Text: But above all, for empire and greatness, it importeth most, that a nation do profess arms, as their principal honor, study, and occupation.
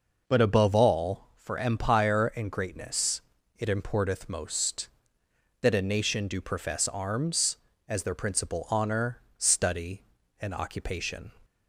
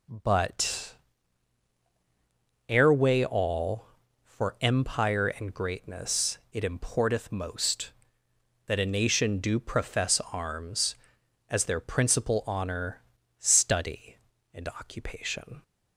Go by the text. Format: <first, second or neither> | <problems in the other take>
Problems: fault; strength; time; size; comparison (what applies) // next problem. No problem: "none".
first | says "airway" for "above"; at 2.6 s